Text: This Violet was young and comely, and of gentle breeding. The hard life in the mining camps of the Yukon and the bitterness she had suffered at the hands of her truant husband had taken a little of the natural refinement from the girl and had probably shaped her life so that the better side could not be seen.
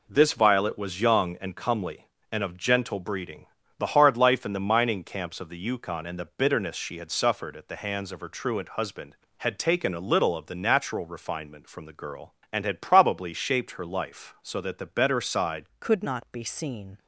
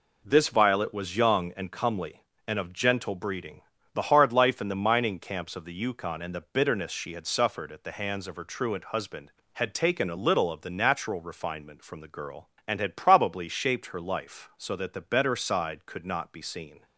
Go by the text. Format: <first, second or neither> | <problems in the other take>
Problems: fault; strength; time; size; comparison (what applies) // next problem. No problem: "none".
second | changes voice at "could"; from 15.8 s on; 1.1 s long